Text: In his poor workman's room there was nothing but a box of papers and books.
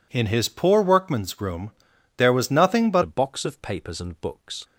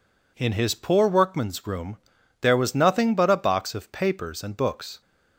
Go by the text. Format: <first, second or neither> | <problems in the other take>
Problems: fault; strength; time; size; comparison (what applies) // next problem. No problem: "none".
second | pauses between "room" and "there"; noticeable; at 1.7 s; 0.46 s long; also in the second // changes voice at "a"; from 3.0 s on; 1.6 s long